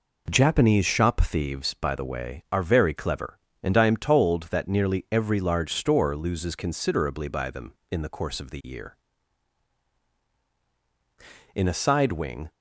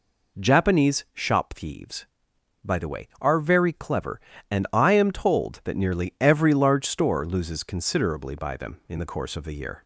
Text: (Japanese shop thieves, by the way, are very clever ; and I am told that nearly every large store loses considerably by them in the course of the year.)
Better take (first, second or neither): second